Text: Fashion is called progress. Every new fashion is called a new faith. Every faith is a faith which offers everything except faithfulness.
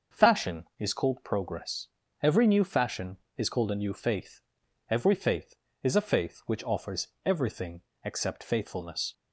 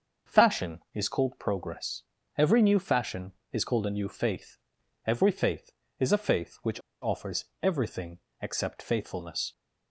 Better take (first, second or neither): first